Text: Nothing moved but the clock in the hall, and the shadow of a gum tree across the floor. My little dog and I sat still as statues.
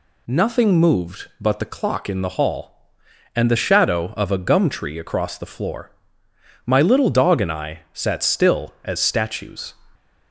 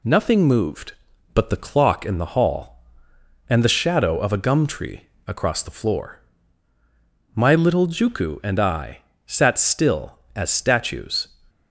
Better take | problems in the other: first | pauses between "tree" and "across"; slight; at 5.0 s; 0.20 s long // says "juku" for "dog"; at 7.8 s // pauses between "I" and "sat"; slight; at 8.9 s; 0.28 s long

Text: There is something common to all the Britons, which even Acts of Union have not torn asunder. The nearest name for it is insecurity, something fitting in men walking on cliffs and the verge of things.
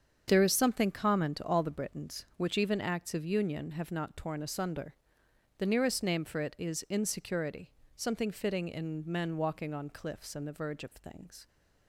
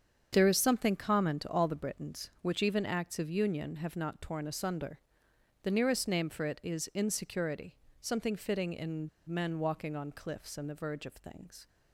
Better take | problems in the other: first | starts louder than the rest; strong; until 1.3 s; 7.5 dB; strong in the first // pauses between "in" and "men"; slight; at 9.0 s; 0.19 s long

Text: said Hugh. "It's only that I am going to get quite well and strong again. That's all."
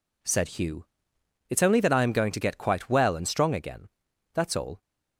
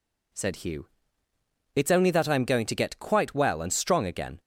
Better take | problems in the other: first | stops before "That's all"; at 4.3 s

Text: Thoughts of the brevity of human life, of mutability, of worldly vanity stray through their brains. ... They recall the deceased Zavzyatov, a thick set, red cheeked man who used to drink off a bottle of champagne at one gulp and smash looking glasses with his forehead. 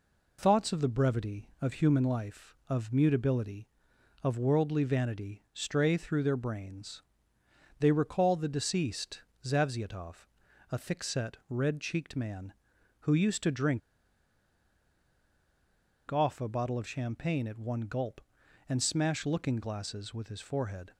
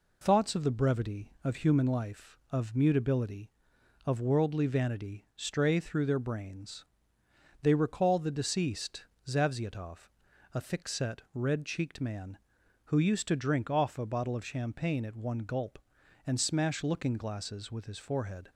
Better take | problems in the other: second | pauses between "deceased" and "Zavzyatov"; slight; at 9.1 s; 0.24 s long; slight in the second // pauses between "drink" and "off"; strong; at 13.8 s; 2.3 s long

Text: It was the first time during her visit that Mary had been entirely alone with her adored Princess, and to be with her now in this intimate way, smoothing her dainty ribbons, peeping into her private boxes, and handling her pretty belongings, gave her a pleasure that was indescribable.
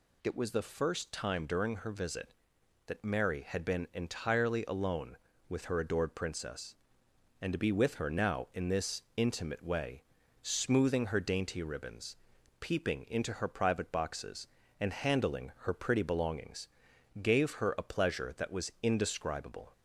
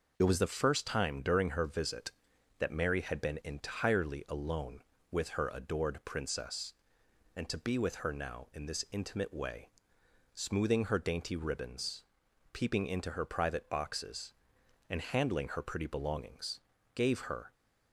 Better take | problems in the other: first | stops before "a pleasure that was indescribable"; at 17.5 s

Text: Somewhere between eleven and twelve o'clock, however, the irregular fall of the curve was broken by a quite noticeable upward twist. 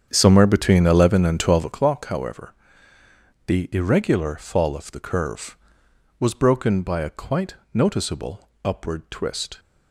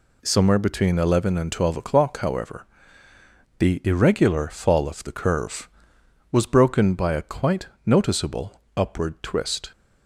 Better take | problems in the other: second | starts louder than the rest; strong; until 1.8 s; 8 dB // pauses between "quite" and "noticeable"; slight; at 7.5 s; 0.18 s long; slight in the second // pauses between "noticeable" and "upward"; slight; at 8.4 s; 0.16 s long; slight in the second

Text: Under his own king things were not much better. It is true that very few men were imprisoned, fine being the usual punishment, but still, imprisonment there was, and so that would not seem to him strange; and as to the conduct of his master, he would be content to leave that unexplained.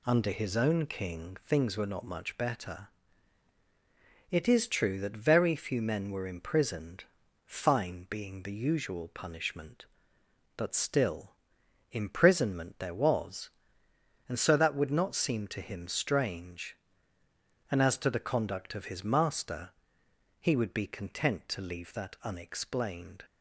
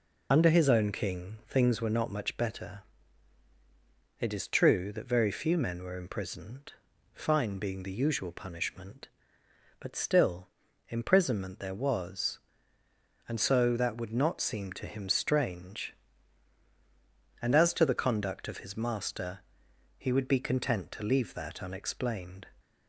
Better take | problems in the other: first | loses the start of "Under"; at 0.3 s; 40 ms

